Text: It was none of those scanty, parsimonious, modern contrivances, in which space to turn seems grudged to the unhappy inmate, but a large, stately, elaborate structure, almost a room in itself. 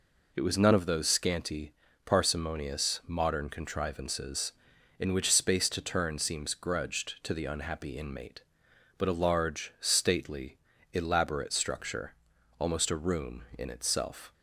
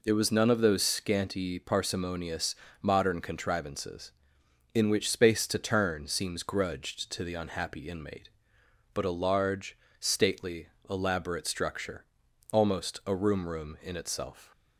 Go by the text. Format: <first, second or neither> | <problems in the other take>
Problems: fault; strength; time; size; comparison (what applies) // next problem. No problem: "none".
first | says "room" twice; at 13.4 s